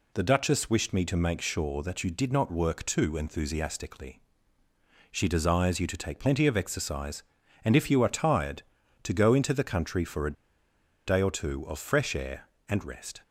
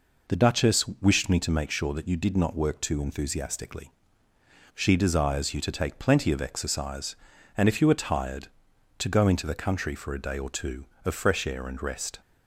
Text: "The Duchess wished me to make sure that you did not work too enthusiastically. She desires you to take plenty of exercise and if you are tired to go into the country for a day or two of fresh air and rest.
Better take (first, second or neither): second